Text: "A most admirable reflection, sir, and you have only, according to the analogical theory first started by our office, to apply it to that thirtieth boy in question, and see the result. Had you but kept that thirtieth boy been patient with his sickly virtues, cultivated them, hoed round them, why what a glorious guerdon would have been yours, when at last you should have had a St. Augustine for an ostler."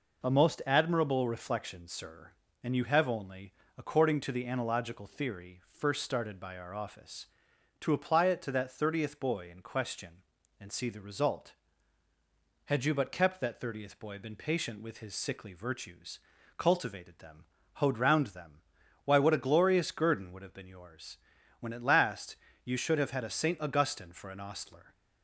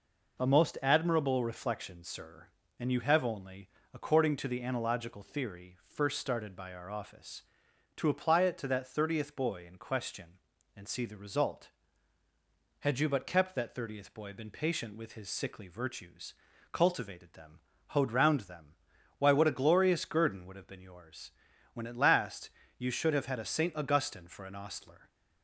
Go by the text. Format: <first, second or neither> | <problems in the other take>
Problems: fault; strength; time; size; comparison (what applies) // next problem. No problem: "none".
neither | pauses between "last" and "you"; slight; the same in both